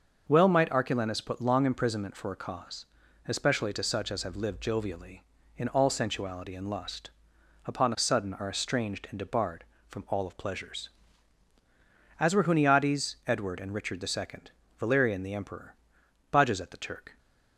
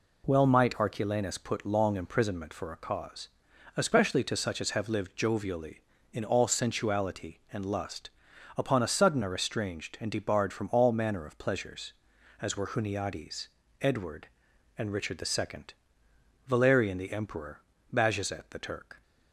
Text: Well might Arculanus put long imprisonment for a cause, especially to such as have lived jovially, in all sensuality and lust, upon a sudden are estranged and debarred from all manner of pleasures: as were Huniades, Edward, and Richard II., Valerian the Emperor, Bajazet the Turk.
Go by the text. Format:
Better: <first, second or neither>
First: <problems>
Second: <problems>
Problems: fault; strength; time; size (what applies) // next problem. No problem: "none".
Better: second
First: starts louder than the rest; until 1.3 s; 6 dB // skips "manner"; at 10.2 s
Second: none